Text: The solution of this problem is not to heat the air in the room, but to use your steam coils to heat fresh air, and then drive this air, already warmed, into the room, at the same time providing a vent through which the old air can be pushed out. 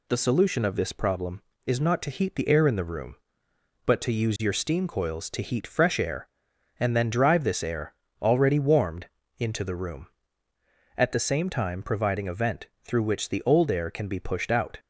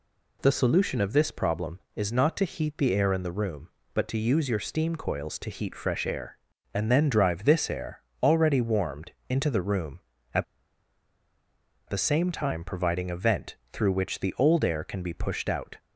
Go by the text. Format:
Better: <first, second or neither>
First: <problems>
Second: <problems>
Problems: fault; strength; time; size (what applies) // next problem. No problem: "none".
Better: first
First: pauses between "vent" and "through"; slight; at 12.6 s; 0.16 s long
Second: pauses between "at" and "the"; strong; at 10.4 s; 1.4 s long // pauses between "vent" and "through"; slight; at 13.5 s; 0.16 s long